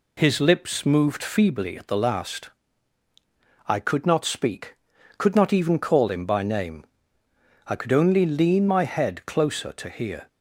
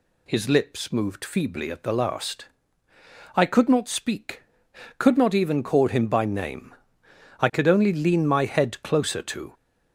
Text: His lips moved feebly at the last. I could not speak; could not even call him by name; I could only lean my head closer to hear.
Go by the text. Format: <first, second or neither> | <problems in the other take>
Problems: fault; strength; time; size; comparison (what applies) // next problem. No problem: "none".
first | stops before "hear"; at 9.5 s